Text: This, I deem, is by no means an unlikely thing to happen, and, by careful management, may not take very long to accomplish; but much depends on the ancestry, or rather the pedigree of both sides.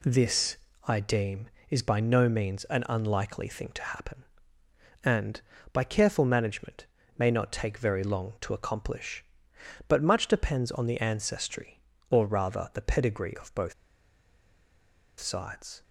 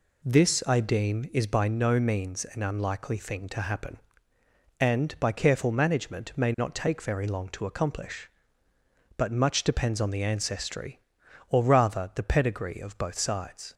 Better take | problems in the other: second | pauses between "both" and "sides"; strong; at 13.7 s; 1.4 s long

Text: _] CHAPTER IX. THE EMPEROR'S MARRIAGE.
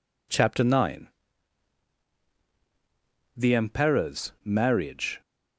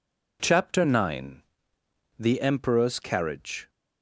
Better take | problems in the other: first | says "Carriage" for "MARRIAGE"; at 3.0 s

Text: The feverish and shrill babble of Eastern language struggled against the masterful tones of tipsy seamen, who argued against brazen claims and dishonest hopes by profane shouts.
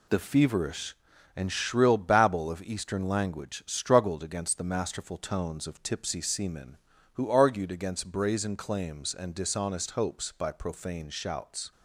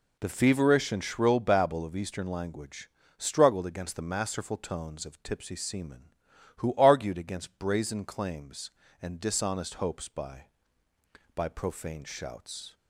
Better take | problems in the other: first | pauses between "language" and "struggled"; slight; at 2.8 s; 0.30 s long // says "by" twice; at 11.3 s

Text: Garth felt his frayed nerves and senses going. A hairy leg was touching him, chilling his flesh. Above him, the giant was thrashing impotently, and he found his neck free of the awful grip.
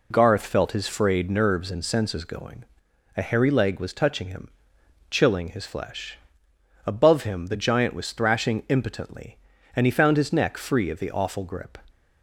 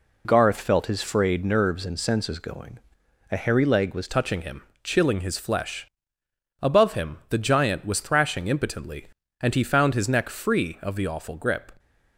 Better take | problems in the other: first | changes voice at "touching"; from 4.0 s on; 7.7 s long

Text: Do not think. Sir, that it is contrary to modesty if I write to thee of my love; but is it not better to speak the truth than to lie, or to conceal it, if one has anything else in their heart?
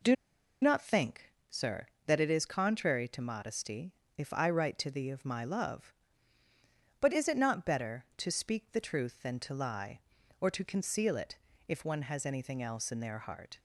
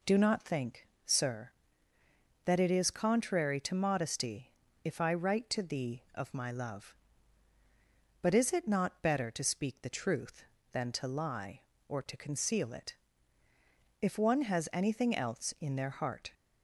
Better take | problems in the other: second | pauses between "Do" and "not"; noticeable; at 0.1 s; 0.47 s long // pauses between "modesty" and "if"; slight; at 3.9 s; 0.26 s long; slight in the second

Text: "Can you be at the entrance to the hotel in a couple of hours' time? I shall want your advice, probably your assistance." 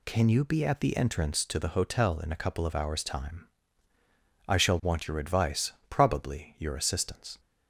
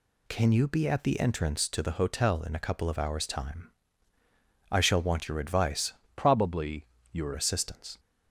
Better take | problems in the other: first | changes voice from "probably" to "your"; from 6.1 to 7.3 s; 1.2 s long // pauses between "probably" and "your"; slight; at 6.8 s; 0.26 s long

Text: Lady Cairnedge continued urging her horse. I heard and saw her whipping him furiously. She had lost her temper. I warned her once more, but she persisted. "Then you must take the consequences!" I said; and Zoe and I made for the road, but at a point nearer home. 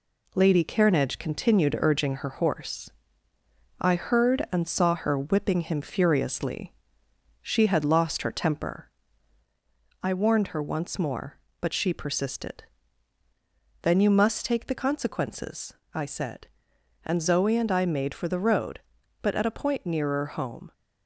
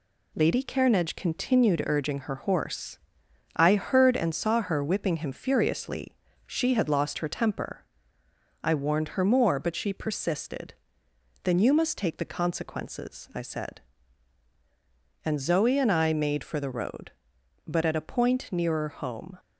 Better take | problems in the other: first | skips "once"; at 9.2 s

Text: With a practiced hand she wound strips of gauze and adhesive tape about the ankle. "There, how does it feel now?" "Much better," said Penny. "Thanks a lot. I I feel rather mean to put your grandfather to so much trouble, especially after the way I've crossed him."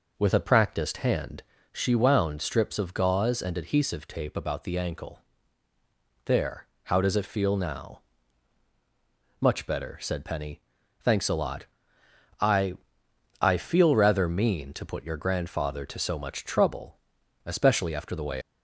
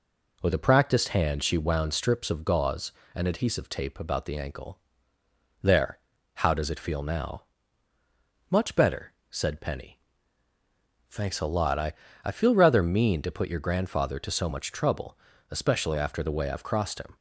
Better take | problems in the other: second | pauses between "hand" and "she"; slight; at 1.4 s; 0.30 s long // pauses between "I" and "I"; noticeable; at 12.7 s; 0.64 s long; slight in the second // stops before "I've crossed him"; at 18.4 s

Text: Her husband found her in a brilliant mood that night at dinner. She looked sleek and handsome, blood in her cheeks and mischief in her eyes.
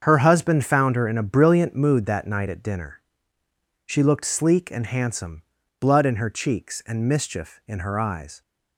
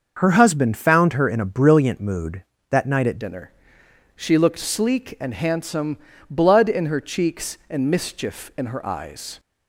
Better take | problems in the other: first | starts louder than the rest; until 1.1 s; 6 dB; also in the first // changes voice at "dinner"; from 3.1 s on; 6.2 s long

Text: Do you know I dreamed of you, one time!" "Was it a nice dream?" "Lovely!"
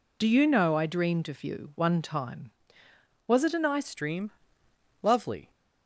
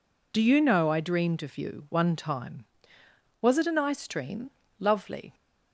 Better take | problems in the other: second | changes voice at "dream"; from 3.9 s on; 1.5 s long

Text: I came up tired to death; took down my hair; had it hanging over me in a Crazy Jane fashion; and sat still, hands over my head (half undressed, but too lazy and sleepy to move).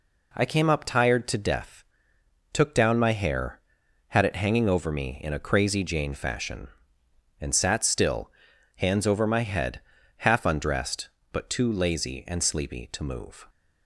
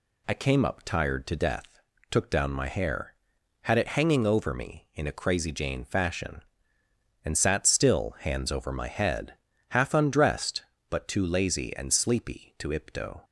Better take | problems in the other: first | says "ipto" for "move"; at 12.7 s

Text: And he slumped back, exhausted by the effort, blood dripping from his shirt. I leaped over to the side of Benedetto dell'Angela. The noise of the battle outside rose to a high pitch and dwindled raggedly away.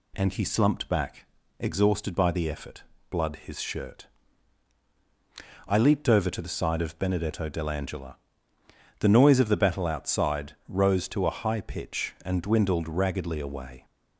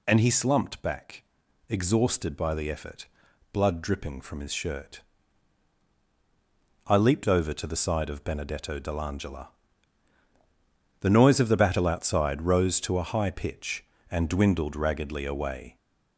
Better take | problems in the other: second | skips "dripping from"; at 3.3 s // pauses between "outside" and "rose"; slight; at 10.5 s; 0.16 s long

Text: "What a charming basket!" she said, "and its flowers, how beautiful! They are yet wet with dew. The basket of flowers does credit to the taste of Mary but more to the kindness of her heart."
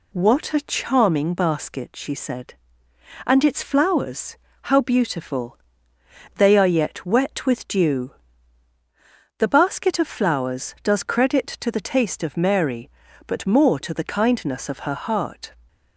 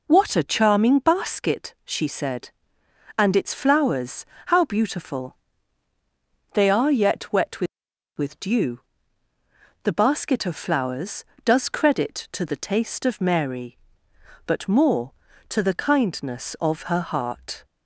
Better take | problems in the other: first | says "with" twice; at 8.1 s

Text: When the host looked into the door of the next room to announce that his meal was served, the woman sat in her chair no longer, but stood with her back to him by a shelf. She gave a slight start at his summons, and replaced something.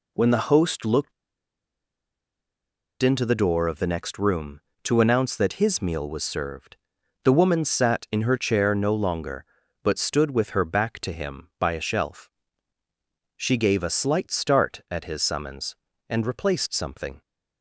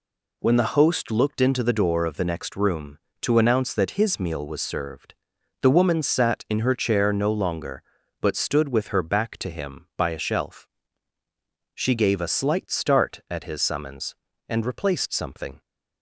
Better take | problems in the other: second | pauses between "looked" and "into"; strong; at 1.1 s; 1.8 s long

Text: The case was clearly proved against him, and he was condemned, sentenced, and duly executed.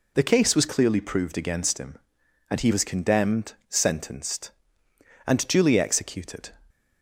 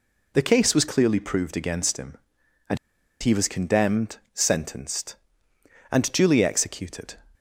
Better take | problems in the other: first | pauses between "and" and "he"; at 2.7 s; 0.43 s long

